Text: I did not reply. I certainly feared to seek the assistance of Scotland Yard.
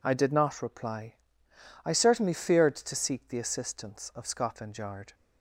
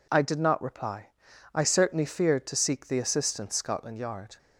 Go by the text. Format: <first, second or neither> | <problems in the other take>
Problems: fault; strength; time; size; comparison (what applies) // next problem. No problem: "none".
first | skips "of"; at 3.5 s